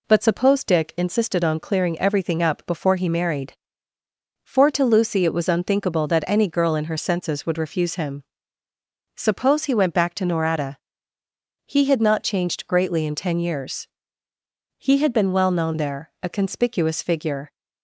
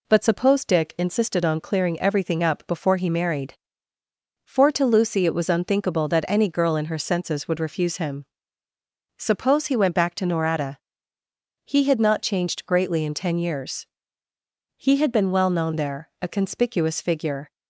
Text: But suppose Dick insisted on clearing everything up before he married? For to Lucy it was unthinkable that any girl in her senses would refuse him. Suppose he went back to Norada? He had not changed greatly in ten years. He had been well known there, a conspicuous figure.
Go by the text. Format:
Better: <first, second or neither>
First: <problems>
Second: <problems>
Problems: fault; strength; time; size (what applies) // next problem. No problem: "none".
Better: neither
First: none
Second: none